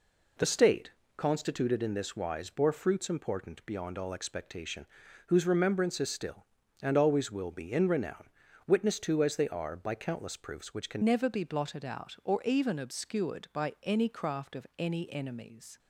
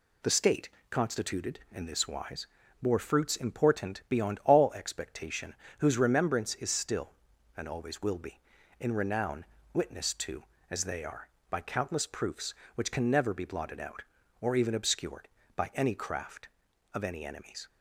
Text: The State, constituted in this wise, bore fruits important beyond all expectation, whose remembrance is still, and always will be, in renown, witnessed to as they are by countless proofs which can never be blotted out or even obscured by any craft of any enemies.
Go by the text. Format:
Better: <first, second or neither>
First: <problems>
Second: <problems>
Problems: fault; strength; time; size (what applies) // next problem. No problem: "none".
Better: second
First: changes voice at "never"; from 11.0 s on; 4.7 s long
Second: none